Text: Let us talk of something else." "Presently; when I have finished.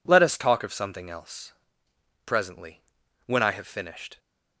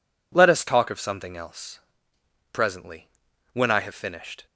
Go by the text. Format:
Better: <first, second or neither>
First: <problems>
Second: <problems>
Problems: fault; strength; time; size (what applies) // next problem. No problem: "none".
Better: neither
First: none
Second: none